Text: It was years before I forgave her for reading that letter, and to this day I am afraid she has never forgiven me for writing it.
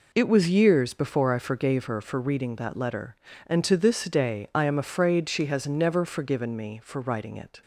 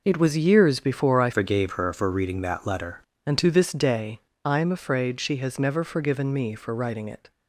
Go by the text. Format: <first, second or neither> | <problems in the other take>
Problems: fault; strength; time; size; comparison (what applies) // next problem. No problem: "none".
first | changes voice from "forgave" to "letter"; from 1.3 to 2.9 s; 1.6 s long // pauses between "day" and "I"; slight; at 4.1 s; 0.26 s long